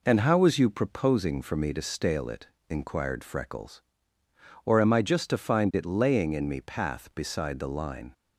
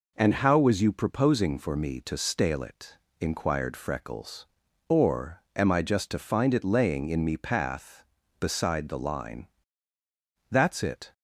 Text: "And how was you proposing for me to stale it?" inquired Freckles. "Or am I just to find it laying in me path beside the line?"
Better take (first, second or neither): first